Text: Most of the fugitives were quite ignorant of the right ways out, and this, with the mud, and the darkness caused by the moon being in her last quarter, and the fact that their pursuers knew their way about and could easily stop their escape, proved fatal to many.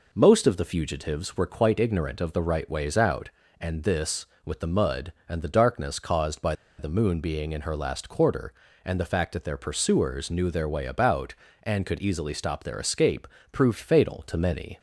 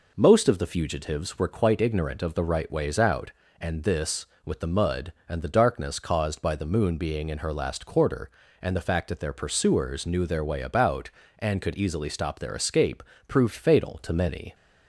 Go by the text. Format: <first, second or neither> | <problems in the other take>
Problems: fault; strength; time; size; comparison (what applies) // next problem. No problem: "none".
second | pauses between "by" and "the"; slight; at 6.5 s; 0.24 s long